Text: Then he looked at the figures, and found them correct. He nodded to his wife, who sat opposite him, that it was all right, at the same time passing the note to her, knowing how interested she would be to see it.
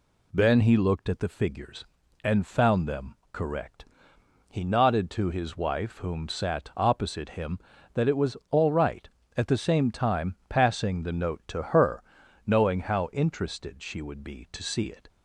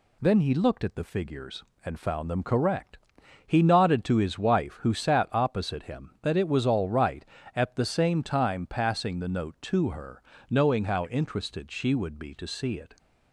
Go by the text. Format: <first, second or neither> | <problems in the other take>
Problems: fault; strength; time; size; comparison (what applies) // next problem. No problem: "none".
second | pauses between "them" and "correct"; slight; at 3.1 s; 0.18 s long // says "whom" for "who"; at 5.9 s